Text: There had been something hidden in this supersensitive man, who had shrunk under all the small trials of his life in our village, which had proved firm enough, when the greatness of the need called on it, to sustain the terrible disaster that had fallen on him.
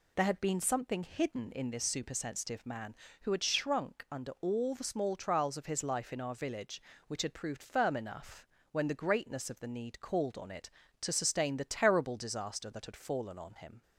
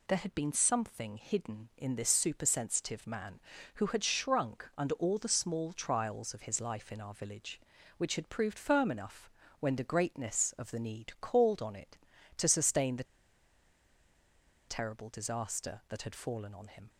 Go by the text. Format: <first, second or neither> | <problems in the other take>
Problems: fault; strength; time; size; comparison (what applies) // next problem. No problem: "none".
first | pauses between "the" and "terrible"; strong; at 13.0 s; 1.6 s long